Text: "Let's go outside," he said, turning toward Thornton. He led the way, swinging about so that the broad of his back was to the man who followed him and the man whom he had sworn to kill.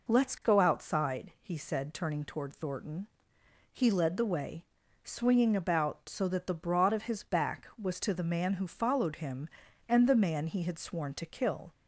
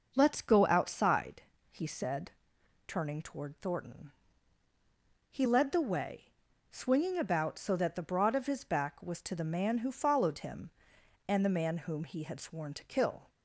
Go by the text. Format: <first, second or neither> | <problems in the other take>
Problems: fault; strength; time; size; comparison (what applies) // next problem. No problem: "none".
second | skips "whom"; at 10.4 s